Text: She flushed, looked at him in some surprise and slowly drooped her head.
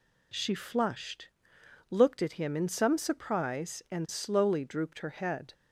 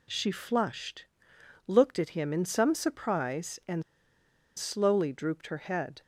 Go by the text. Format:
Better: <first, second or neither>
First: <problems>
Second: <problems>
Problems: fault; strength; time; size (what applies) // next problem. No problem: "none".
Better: first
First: none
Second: pauses between "and" and "slowly"; noticeable; at 3.8 s; 0.75 s long